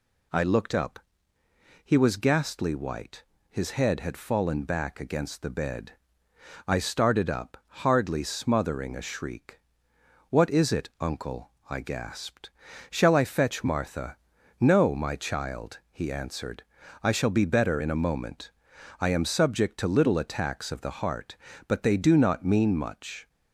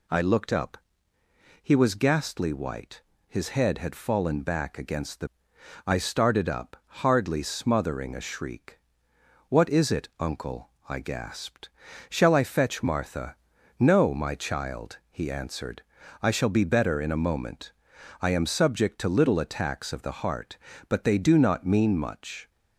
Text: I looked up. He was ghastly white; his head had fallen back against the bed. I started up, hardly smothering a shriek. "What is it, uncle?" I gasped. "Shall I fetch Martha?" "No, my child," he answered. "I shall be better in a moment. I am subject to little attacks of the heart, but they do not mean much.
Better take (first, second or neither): first